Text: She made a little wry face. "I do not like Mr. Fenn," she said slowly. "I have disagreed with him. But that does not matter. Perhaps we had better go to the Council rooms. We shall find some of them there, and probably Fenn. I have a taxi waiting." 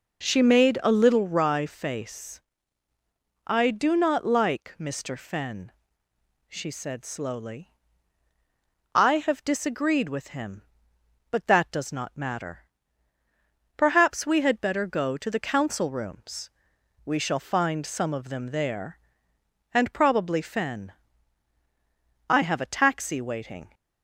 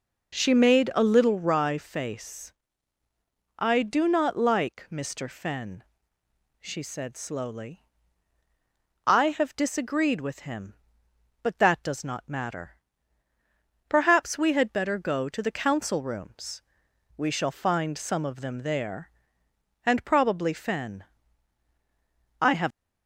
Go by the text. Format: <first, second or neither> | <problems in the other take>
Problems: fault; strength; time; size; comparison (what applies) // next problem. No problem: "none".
first | stops before "a taxi waiting"; at 22.7 s